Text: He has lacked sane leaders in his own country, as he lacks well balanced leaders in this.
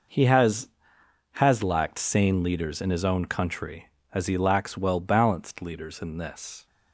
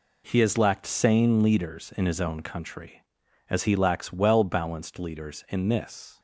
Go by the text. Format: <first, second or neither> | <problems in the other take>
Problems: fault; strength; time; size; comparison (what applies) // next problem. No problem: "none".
second | says "has" twice; at 1.3 s